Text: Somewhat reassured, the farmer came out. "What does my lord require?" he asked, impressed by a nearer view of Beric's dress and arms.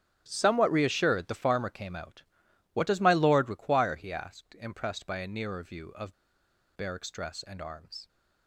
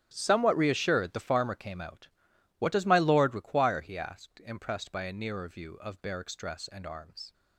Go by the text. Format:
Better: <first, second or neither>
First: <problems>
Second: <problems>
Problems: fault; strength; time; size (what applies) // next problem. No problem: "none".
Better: second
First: starts louder than the rest; strong; until 1.2 s; 10 dB // pauses between "of" and "Beric's"; noticeable; at 6.1 s; 0.63 s long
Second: starts louder than the rest; strong; until 1.1 s; 10 dB